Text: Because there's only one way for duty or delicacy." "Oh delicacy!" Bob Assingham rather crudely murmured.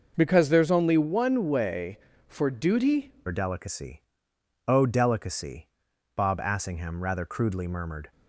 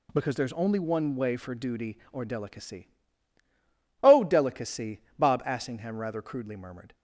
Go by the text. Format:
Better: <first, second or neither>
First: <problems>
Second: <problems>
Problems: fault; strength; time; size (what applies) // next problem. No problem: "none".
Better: second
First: changes voice at "or"; from 3.2 s on; 4.9 s long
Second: none